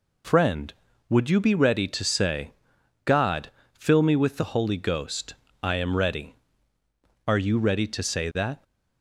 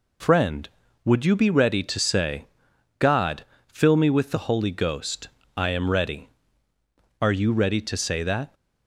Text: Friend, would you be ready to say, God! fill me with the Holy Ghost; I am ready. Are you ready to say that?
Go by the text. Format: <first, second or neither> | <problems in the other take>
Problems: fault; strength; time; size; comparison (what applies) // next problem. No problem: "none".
neither | none